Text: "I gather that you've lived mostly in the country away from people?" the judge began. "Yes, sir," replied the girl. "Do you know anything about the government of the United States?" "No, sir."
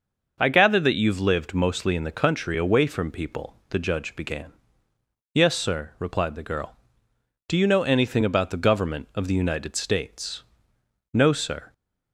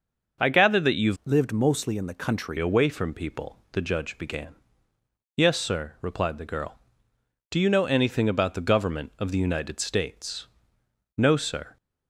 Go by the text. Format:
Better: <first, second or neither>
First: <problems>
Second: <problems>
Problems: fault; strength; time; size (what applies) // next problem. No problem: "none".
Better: first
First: starts louder than the rest; noticeable; until 1.3 s; 6 dB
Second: starts louder than the rest; noticeable; until 1.4 s; 6 dB // changes voice from "lived" to "country"; from 1.2 to 2.5 s; 1.3 s long